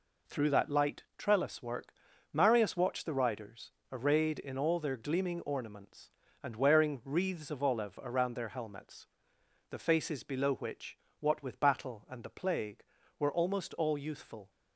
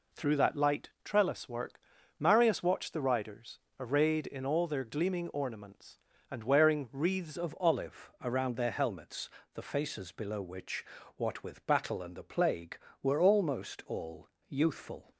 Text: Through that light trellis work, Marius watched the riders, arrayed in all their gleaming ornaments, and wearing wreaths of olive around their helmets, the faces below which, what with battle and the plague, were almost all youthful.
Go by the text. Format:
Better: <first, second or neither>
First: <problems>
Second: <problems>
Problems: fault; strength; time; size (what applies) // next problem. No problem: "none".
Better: first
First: none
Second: changes voice at "of"; from 7.3 s on; 7.8 s long // pauses between "all" and "youthful"; slight; at 14.2 s; 0.20 s long